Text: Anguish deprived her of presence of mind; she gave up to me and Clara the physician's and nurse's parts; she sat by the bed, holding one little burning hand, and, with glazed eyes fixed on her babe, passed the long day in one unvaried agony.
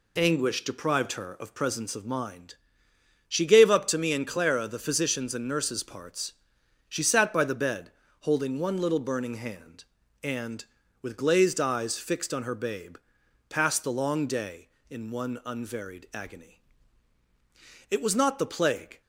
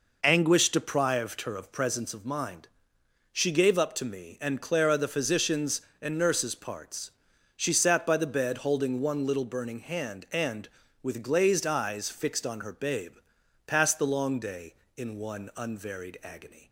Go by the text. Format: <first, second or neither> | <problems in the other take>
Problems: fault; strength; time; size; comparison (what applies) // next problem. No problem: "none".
second | goes on to say "It was not the plague"; noticeable; from 17.9 s on; 1.1 s long